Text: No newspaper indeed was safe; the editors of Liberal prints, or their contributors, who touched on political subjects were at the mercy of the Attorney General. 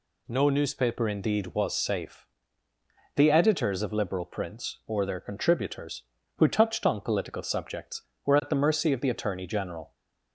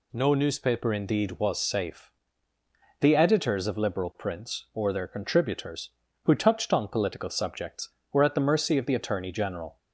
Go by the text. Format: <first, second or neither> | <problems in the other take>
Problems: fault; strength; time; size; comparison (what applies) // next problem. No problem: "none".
neither | none